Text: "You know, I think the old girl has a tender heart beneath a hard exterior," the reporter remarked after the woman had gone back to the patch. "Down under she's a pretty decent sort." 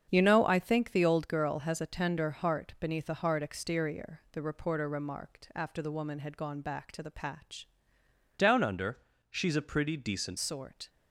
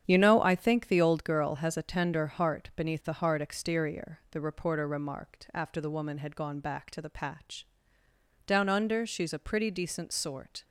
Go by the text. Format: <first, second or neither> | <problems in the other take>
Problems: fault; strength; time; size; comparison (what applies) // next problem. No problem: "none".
second | starts louder than the rest; strong; until 1.1 s; 7.5 dB; strong in the second // changes voice from "Down" to "decent"; from 8.3 to 10.3 s; 2.0 s long // pauses between "under" and "she's"; slight; at 8.9 s; 0.32 s long